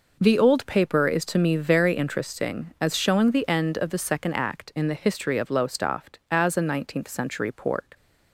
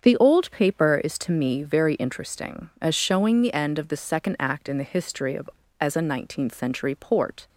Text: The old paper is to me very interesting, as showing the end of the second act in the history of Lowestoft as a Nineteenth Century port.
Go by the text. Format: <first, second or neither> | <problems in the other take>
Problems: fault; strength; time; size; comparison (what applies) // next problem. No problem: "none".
first | starts louder than the rest; strong; until 1.0 s; 7.5 dB // skips "Lowestoft"; at 5.6 s